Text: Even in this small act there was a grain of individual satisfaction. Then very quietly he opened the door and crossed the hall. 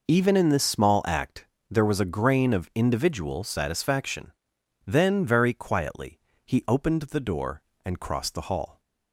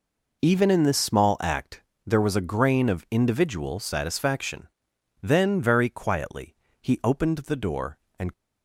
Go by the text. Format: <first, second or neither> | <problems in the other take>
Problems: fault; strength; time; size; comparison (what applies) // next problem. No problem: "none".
first | pauses between "act" and "there"; slight; at 1.8 s; 0.24 s long; slight in the first // pauses between "quietly" and "he"; slight; at 6.5 s; 0.24 s long; slight in the first // stops before "crossed the hall"; at 8.3 s